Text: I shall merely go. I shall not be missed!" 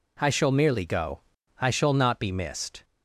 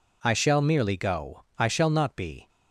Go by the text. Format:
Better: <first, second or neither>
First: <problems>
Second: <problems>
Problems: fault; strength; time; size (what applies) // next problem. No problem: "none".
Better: first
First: none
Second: stops before "missed"; at 2.4 s